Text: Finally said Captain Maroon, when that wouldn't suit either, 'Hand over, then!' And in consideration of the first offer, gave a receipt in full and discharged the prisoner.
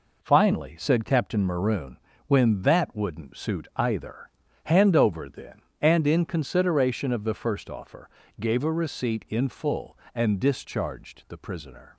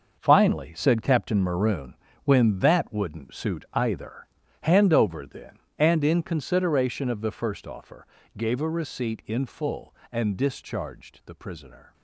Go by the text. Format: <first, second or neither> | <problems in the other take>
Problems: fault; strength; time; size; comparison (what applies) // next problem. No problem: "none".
first | gets quieter; strong; throughout; 10.5 dB